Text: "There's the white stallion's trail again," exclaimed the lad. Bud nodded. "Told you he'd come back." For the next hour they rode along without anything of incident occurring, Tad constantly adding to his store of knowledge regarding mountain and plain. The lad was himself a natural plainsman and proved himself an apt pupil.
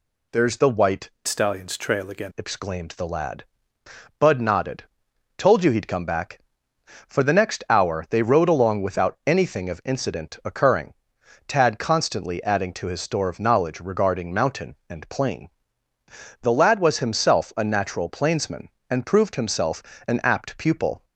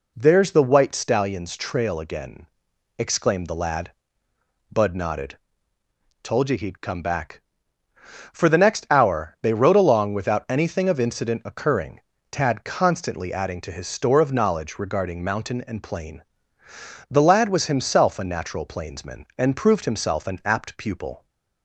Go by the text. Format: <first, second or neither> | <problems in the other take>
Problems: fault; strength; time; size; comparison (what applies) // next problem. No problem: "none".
second | changes voice from "stallion's" to "again"; from 1.2 to 2.3 s; 1.1 s long // pauses between "himself" and "an"; slight; at 19.8 s; 0.24 s long